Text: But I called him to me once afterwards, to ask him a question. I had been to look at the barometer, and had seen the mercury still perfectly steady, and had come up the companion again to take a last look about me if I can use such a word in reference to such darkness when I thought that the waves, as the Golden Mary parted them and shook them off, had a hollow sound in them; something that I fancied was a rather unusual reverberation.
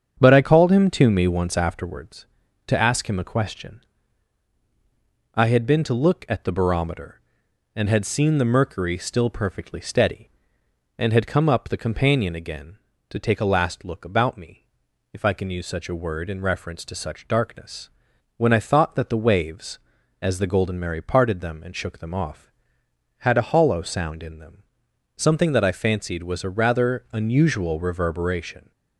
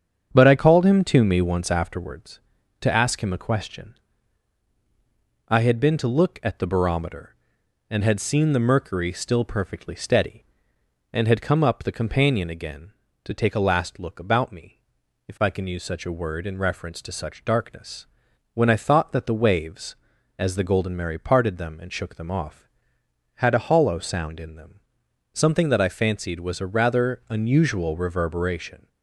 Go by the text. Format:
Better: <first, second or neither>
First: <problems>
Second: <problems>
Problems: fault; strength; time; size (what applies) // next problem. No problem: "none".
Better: neither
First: starts louder than the rest; strong; until 1.2 s; 8 dB // pauses between "me" and "if"; noticeable; at 14.6 s; 0.50 s long // pauses between "darkness" and "when"; noticeable; at 17.8 s; 0.48 s long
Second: starts louder than the rest; strong; until 1.3 s; 8 dB // pauses between "me" and "if"; noticeable; at 14.7 s; 0.50 s long // pauses between "darkness" and "when"; noticeable; at 18.0 s; 0.48 s long